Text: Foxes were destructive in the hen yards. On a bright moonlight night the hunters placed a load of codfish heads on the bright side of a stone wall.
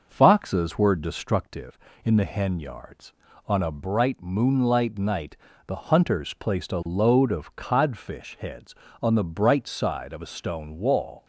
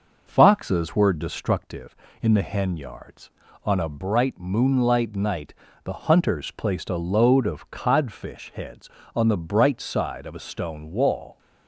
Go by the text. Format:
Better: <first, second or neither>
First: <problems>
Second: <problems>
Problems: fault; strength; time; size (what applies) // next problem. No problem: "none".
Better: neither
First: pauses between "night" and "the"; slight; at 5.3 s; 0.32 s long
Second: pauses between "night" and "the"; slight; at 5.5 s; 0.32 s long